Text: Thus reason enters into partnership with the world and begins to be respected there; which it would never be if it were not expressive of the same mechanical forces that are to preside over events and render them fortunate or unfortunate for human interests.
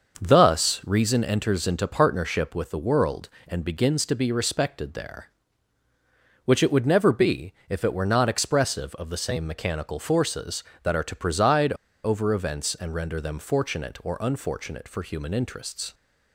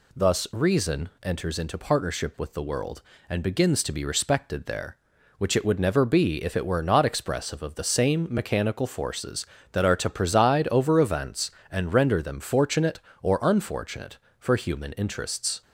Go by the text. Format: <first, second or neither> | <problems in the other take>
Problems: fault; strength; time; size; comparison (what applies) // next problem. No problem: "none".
second | starts louder than the rest; until 1.2 s; 6 dB // pauses between "be" and "if"; slight; at 7.5 s; 0.16 s long // pauses between "preside" and "over"; slight; at 11.7 s; 0.30 s long